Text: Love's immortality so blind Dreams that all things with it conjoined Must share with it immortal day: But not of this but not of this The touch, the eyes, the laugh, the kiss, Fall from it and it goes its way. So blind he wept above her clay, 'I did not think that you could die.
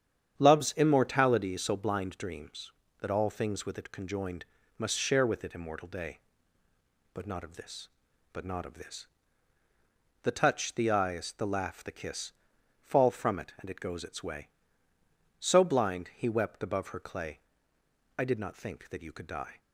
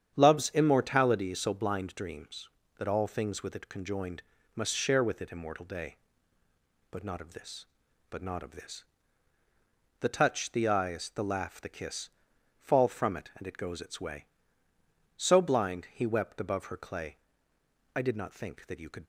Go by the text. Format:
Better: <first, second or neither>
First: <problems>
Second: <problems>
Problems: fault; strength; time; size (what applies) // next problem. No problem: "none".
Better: first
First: starts louder than the rest; strong; until 1.4 s; 8.5 dB // pauses between "conjoined" and "Must"; slight; at 4.4 s; 0.34 s long // pauses between "this" and "The"; at 9.0 s; 1.1 s long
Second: starts louder than the rest; strong; until 1.1 s; 8.5 dB // pauses between "conjoined" and "Must"; slight; at 4.2 s; 0.34 s long // pauses between "this" and "The"; at 8.8 s; 1.1 s long // stops before "die"; at 19.0 s